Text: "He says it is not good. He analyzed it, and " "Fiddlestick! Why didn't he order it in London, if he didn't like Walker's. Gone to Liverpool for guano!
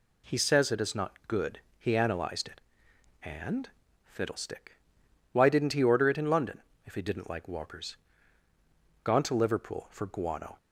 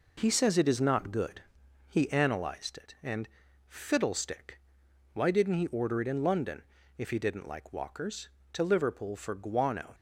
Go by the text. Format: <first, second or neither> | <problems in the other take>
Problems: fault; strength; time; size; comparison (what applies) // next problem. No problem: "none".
first | skips "Gone"; at 8.4 s